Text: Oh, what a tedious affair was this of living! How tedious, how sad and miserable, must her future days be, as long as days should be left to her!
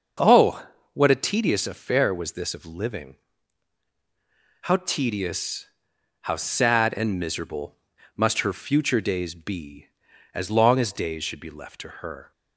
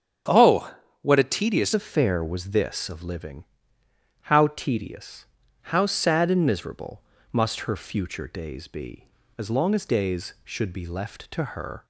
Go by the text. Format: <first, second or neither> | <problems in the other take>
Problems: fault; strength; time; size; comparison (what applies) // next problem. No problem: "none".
first | starts louder than the rest; strong; until 1.5 s; 8 dB; also in the first // changes voice at "affair"; from 1.7 s on; 10.1 s long